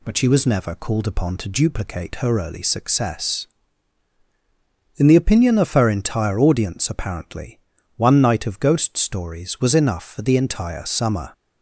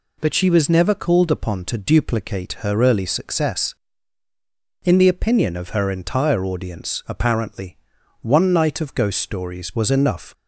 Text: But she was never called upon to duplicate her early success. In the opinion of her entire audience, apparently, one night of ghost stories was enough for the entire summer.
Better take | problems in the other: first | stops before "for the entire summer"; at 10.3 s

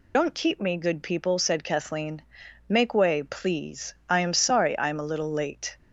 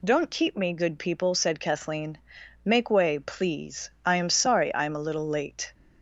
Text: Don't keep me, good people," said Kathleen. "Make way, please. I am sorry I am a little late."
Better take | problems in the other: second | loses the start of "Don't"; at 0.1 s; 85 ms

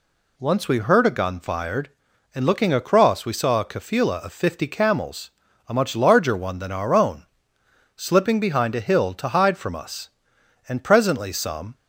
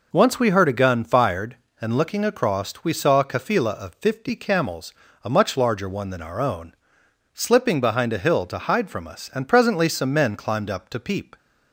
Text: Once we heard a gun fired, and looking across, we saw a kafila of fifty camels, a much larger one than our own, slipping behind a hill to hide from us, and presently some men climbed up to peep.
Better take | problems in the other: second | stops before "men climbed up to peep"; at 11.7 s

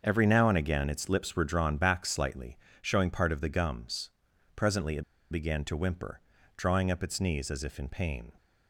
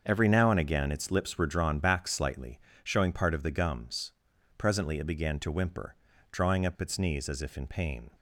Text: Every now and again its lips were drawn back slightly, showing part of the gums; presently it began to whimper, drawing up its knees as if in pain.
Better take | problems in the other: second | starts louder than the rest; until 1.0 s; 7 dB; also in the second // pauses between "it" and "began"; slight; at 5.0 s; 0.27 s long

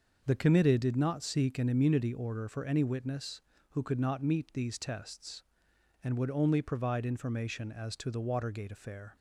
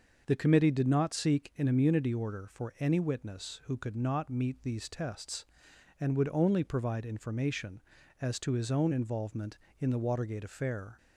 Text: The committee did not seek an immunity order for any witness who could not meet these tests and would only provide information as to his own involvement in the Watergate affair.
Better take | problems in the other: second | starts louder than the rest; until 1.2 s; 6 dB; noticeable in the second // skips "his own involvement in"; at 8.1 s

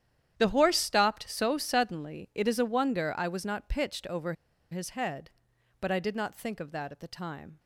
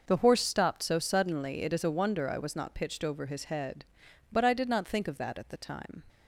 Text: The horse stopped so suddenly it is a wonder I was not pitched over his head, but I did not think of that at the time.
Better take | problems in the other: second | starts louder than the rest; strong; until 1.3 s; 10 dB // pauses between "over" and "his"; at 4.3 s; 0.37 s long

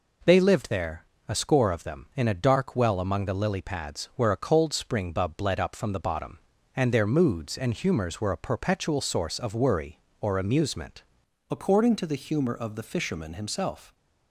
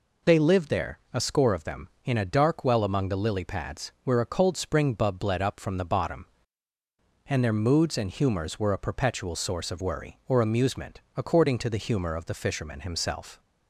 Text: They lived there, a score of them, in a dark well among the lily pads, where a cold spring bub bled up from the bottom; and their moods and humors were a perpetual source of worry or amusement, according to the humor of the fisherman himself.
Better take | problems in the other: second | changes voice at "according"; from 11.4 s on; 2.5 s long

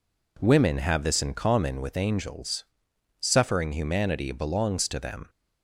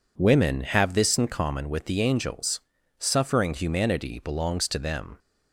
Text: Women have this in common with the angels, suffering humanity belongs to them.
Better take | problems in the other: second | skips "the"; at 1.9 s

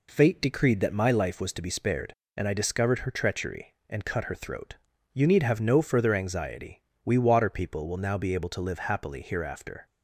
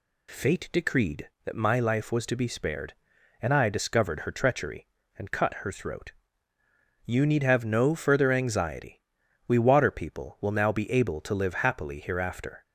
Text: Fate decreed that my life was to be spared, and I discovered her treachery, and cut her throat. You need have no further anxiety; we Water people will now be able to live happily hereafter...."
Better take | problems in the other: neither | none

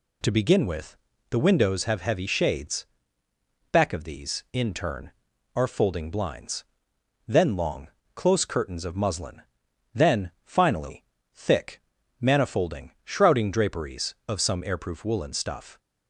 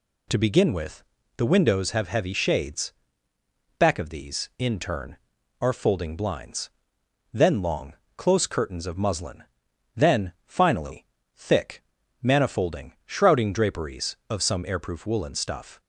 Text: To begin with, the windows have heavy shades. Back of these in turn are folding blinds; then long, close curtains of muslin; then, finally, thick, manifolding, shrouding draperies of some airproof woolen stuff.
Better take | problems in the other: neither | none

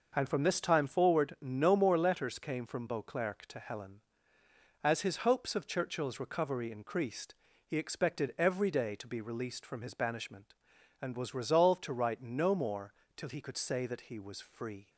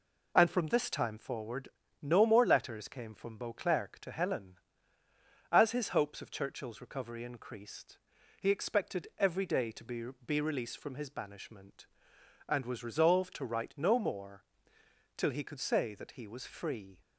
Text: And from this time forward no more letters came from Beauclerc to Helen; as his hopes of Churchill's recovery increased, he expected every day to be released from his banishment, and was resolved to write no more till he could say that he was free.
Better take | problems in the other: first | pauses between "forward" and "no"; slight; at 1.6 s; 0.34 s long // says "be" twice; at 10.2 s // pauses between "more" and "till"; noticeable; at 14.4 s; 0.72 s long; slight in the first

